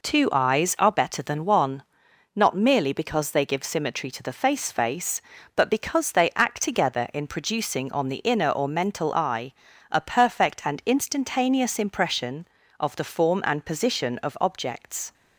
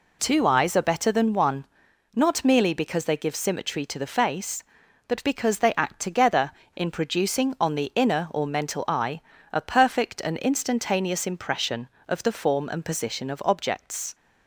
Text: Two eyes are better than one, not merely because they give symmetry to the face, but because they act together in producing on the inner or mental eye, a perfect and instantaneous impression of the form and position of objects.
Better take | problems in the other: second | says "face" twice; at 4.7 s

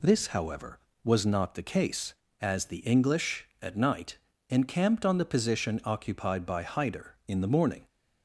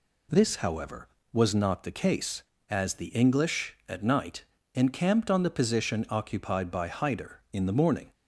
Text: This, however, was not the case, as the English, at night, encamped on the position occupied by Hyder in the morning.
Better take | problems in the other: neither | none

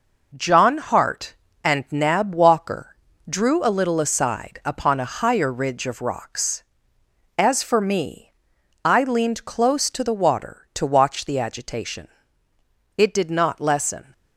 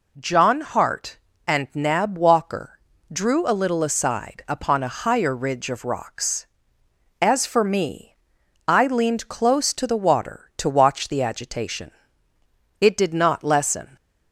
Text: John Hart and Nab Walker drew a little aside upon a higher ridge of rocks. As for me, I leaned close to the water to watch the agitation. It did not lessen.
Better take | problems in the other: second | gets quieter; throughout; 6.5 dB // pauses between "Walker" and "drew"; slight; at 2.9 s; 0.32 s long; slight in the second

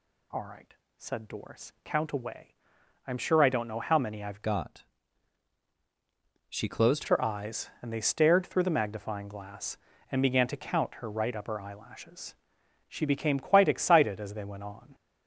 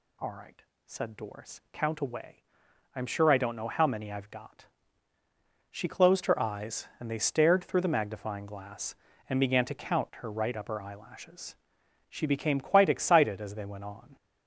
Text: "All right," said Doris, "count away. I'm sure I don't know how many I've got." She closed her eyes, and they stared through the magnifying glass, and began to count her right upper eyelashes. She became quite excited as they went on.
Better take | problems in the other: second | changes voice from "got" to "closed"; from 4.4 to 7.0 s; 2.6 s long

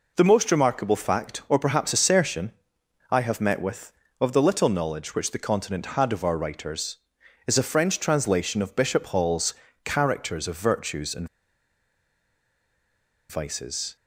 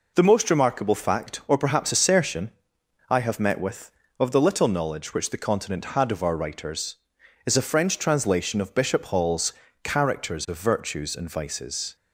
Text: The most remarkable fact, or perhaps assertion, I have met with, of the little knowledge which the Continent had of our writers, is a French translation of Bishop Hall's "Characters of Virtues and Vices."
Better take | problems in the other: second | pauses between "Hall's" and "Characters"; slight; at 9.5 s; 0.32 s long; slight in the second // pauses between "and" and "Vices"; strong; at 11.2 s; 2.0 s long

